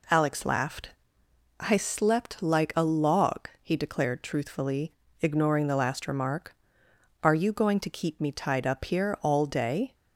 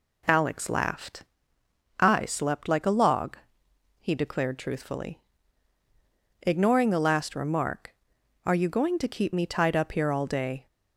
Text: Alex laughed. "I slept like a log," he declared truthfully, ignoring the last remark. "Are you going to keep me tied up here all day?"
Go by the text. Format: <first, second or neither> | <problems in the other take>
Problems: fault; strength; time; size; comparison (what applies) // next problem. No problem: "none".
neither | none